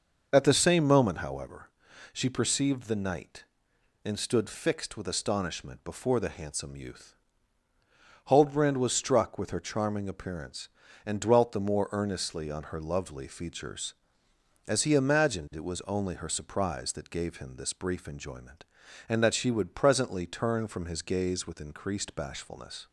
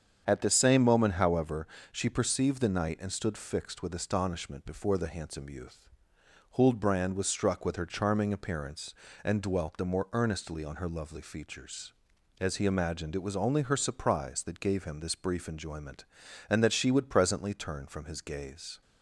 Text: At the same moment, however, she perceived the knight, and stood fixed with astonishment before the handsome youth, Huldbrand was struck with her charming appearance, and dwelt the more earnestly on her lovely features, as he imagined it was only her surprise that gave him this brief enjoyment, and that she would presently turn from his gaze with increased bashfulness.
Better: first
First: starts louder than the rest; noticeable; until 1.3 s; 6 dB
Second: starts louder than the rest; strong; until 1.2 s; 7.5 dB // stops before "with increased bashfulness"; at 18.8 s

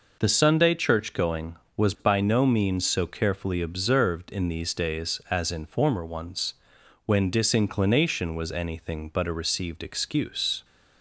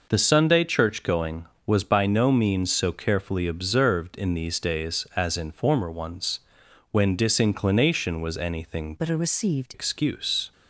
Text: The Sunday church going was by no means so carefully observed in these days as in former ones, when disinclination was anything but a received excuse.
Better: first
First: none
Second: changes voice from "but" to "received"; from 8.9 to 9.7 s; 0.8 s long

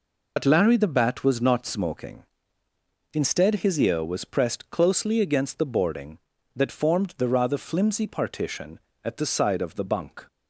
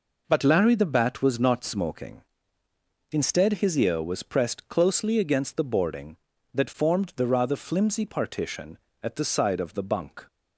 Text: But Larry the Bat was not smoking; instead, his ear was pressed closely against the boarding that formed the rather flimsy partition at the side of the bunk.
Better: second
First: loses the start of "But"; at 0.3 s; 80 ms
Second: none

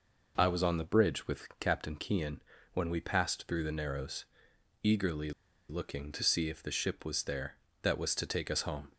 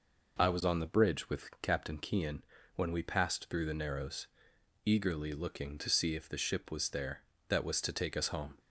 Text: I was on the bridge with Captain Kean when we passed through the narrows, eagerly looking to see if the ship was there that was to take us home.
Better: second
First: pauses between "Kean" and "when"; slight; at 2.4 s; 0.32 s long // pauses between "eagerly" and "looking"; at 5.3 s; 0.38 s long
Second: pauses between "Kean" and "when"; slight; at 2.4 s; 0.32 s long

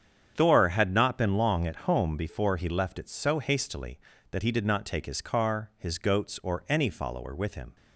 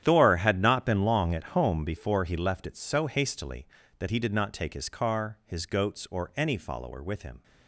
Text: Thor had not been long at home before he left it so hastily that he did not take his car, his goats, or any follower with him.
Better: first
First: starts louder than the rest; strong; until 1.3 s; 8 dB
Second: gets quieter; strong; throughout; 14.5 dB // starts louder than the rest; strong; until 1.0 s; 10.5 dB

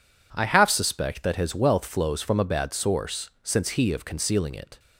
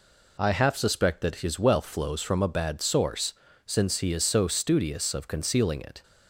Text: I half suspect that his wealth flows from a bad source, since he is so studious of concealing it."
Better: second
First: skips "is so studious"; at 3.9 s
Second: none

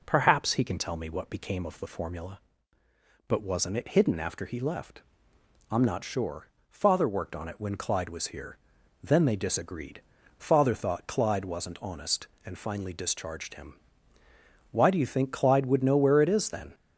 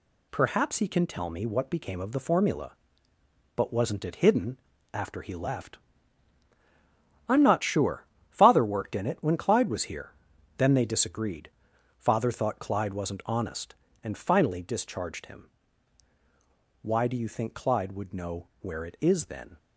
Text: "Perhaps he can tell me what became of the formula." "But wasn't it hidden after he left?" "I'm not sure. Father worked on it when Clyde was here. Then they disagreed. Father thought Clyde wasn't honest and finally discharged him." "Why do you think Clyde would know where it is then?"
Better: first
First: none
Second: pauses between "hidden" and "after"; slight; at 4.5 s; 0.34 s long // says "in" for "on"; at 8.9 s

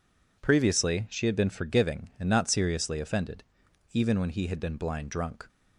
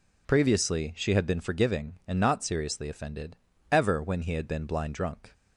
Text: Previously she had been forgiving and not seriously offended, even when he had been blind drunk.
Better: first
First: none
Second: says "ever" for "even"; at 3.7 s

